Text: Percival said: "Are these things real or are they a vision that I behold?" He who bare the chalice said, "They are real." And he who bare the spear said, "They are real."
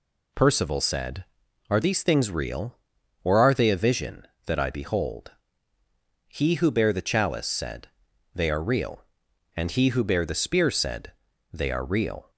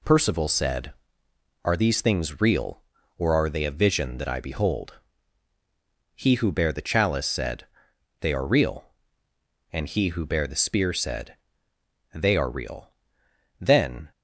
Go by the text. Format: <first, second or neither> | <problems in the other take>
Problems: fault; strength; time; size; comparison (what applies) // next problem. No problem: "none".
first | goes on to say "Then"; from 13.5 s on; 0.52 s long